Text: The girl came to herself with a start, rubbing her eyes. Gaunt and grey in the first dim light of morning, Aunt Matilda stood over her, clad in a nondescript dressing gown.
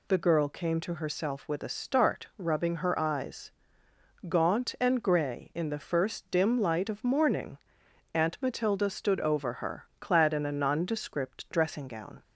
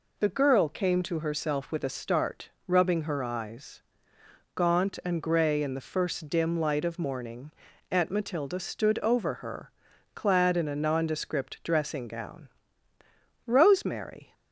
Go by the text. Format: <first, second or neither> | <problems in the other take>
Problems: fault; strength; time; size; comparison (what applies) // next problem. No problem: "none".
first | goes on to say "Rosemary"; noticeable; from 13.4 s on; 0.88 s long